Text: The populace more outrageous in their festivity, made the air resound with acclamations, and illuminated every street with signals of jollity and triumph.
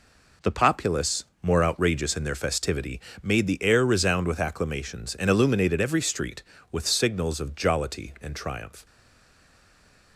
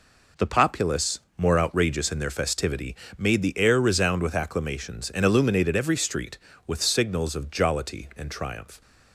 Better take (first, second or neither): second